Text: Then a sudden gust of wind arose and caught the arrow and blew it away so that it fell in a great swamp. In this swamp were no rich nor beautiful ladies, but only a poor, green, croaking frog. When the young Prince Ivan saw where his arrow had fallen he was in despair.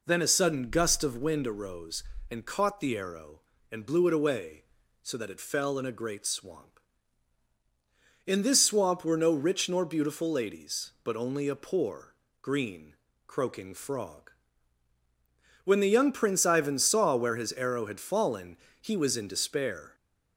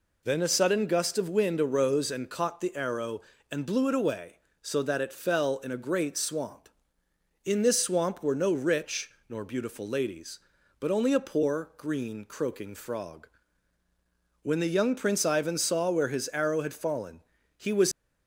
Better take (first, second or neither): first